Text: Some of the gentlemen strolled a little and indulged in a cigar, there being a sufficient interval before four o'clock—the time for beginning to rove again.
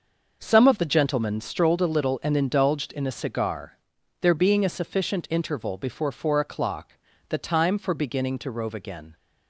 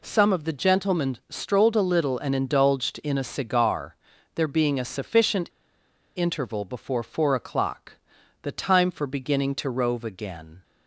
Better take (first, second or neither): first